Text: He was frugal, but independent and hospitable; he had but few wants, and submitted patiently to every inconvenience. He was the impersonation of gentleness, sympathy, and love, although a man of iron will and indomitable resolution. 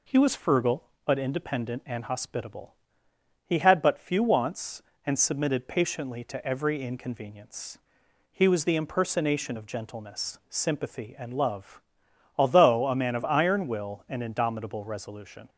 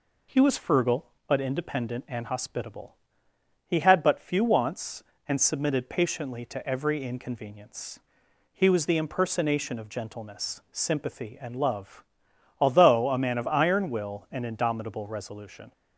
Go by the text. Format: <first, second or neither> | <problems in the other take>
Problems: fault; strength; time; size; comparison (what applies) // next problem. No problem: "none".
neither | none